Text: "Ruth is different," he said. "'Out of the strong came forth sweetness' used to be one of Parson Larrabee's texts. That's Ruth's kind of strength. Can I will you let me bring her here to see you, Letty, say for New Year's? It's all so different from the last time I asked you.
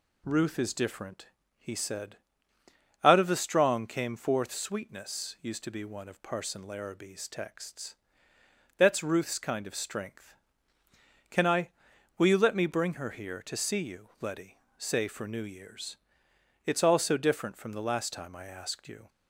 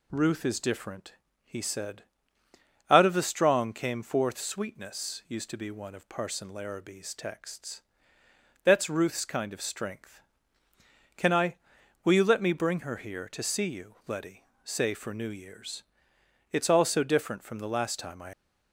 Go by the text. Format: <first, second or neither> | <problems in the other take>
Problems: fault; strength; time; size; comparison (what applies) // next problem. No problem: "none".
first | stops before "asked you"; at 18.3 s